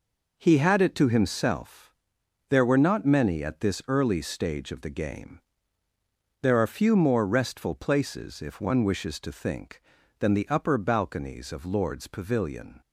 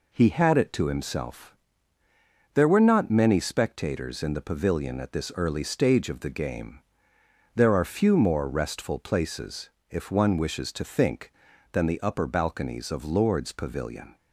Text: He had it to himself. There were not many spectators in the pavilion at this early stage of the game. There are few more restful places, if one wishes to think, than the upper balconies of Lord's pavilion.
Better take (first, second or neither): second